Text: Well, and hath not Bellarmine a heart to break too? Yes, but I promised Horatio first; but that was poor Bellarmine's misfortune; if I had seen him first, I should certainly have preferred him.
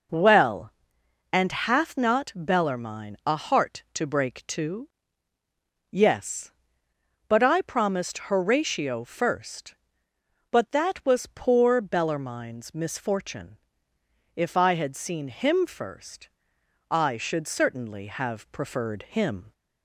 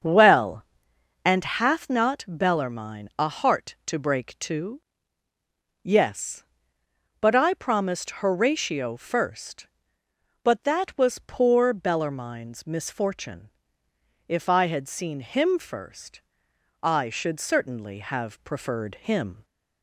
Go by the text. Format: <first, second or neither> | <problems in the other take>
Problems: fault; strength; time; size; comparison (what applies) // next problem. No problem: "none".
first | starts louder than the rest; until 1.4 s; 6.5 dB